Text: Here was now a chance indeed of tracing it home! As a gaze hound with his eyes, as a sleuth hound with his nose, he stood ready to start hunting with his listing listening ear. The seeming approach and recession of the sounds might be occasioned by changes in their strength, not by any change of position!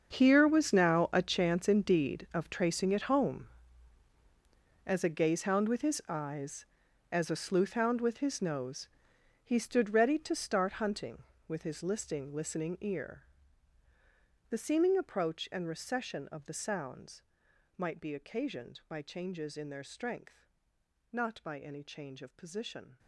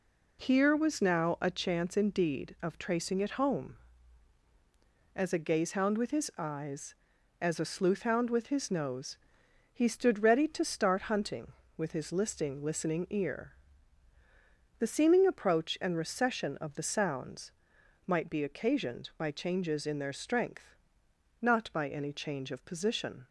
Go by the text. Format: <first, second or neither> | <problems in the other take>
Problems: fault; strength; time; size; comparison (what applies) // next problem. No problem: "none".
second | gets quieter; strong; throughout; 16 dB // pauses between "sounds" and "might"; noticeable; at 17.2 s; 0.54 s long; noticeable in the second